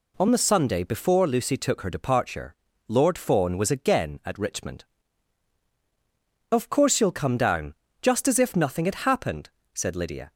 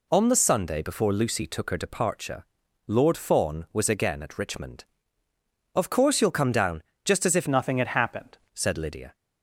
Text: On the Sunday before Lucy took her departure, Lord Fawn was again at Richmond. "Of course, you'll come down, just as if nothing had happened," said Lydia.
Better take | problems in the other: first | changes voice from "nothing" to "happened"; from 7.4 to 8.3 s; 0.9 s long

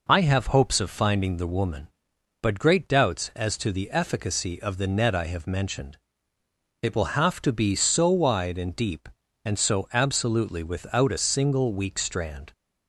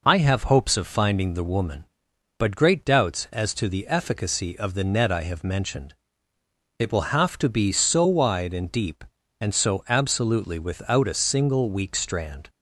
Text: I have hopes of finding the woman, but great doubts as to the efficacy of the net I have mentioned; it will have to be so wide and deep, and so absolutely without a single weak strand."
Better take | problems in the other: neither | none

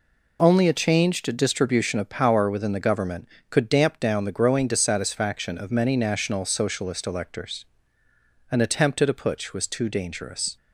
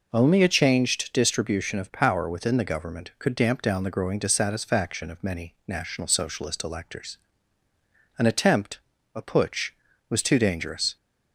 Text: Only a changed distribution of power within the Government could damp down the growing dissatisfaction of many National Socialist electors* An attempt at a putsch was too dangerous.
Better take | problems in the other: first | pauses between "electors" and "An"; at 7.1 s; 1.0 s long; noticeable in the first // skips "at"; at 8.9 s

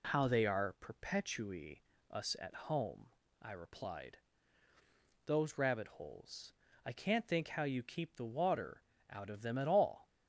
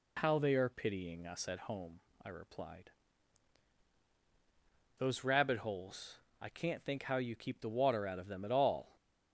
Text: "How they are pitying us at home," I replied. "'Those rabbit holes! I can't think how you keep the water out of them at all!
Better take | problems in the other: second | says "perpetui" for "pitying"; at 0.7 s // pauses between "at" and "home"; slight; at 2.5 s; 0.16 s long // pauses between "water" and "out"; slight; at 8.8 s; 0.26 s long

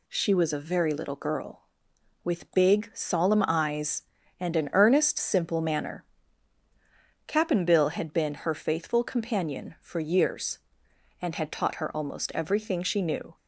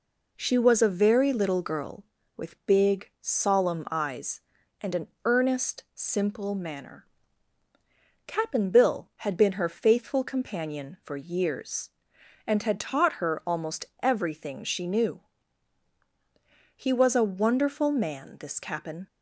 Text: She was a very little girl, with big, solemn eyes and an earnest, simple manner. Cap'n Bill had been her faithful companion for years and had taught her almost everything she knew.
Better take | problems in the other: first | pauses between "an" and "earnest"; slight; at 5.0 s; 0.18 s long // pauses between "almost" and "everything"; slight; at 13.8 s; 0.16 s long // goes on to say "He was a wonderful man this Cap'n"; strong; from 16.7 s on; 2.3 s long

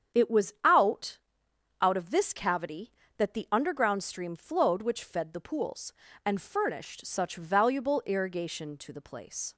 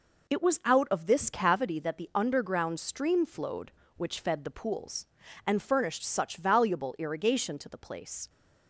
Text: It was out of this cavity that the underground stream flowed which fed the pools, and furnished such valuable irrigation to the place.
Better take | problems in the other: second | starts louder than the rest; strong; until 1.8 s; 8 dB // says "out" twice; at 1.8 s

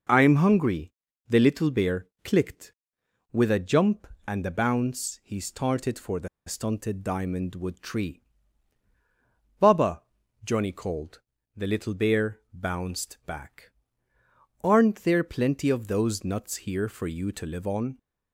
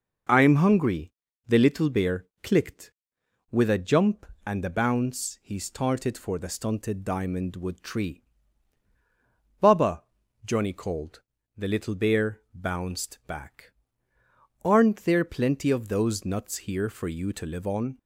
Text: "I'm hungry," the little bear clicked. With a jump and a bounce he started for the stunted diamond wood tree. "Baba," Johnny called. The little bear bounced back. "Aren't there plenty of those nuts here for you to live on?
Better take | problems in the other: second | pauses between "bear" and "clicked"; slight; at 2.0 s; 0.16 s long; slight in the second // pauses between "the" and "stunted"; slight; at 6.2 s; 0.19 s long

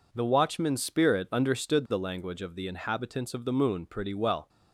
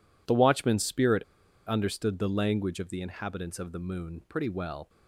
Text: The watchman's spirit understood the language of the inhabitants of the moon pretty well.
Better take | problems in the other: first | pauses between "spirit" and "understood"; at 1.2 s; 0.44 s long

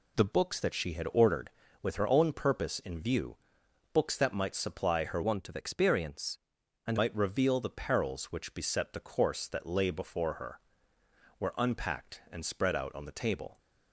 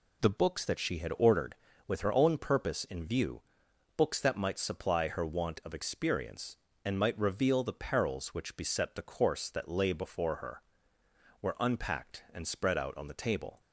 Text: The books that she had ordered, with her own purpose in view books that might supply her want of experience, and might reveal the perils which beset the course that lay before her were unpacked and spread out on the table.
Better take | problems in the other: second | pauses between "view" and "books"; noticeable; at 3.3 s; 0.56 s long; noticeable in the second // changes voice from "want" to "and"; from 5.2 to 6.9 s; 1.7 s long

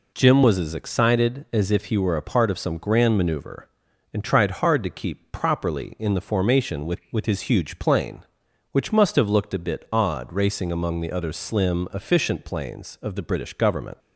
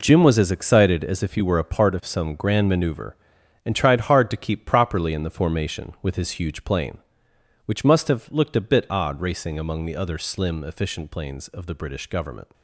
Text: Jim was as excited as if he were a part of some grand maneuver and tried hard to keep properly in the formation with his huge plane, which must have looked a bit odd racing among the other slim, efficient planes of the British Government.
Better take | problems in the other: second | says "with" twice; at 7.1 s

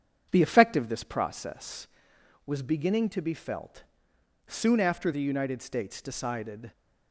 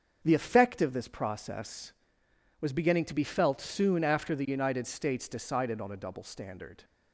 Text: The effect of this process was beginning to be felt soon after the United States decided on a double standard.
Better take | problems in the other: second | starts louder than the rest; strong; until 1.3 s; 8 dB; also in the second // pauses between "felt" and "soon"; noticeable; at 3.8 s; 0.64 s long // stops before "on a double standard"; at 6.7 s

